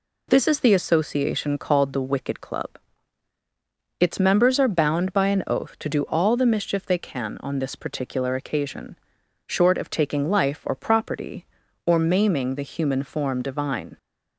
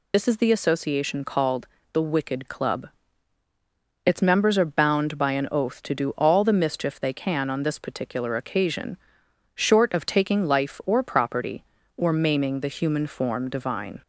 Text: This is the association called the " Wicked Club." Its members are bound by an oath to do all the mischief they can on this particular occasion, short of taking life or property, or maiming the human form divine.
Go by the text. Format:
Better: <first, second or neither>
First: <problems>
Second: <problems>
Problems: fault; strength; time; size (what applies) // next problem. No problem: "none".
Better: first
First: none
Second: loses the start of "This"; at 0.1 s; 45 ms // pauses between "called" and "the"; slight; at 1.6 s; 0.26 s long